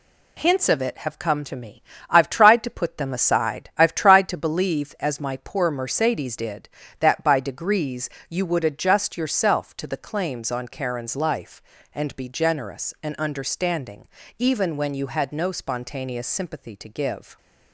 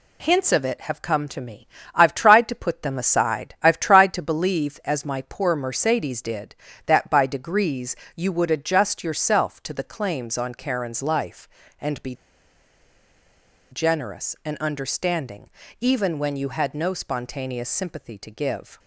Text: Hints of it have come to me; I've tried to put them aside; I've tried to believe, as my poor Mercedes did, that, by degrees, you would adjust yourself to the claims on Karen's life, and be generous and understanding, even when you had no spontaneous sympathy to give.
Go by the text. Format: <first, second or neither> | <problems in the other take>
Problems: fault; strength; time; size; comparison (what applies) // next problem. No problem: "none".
first | pauses between "be" and "generous"; strong; at 12.1 s; 1.5 s long